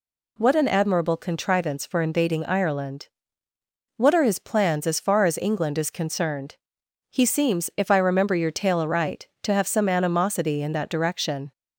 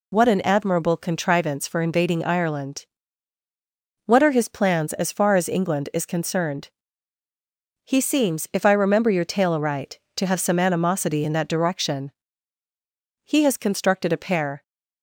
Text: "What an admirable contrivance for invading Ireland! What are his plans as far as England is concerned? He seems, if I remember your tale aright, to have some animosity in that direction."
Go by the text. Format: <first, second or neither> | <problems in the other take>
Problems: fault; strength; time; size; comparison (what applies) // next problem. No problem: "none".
first | goes on to say "He has constructed a pair"; from 13.2 s on; 1.3 s long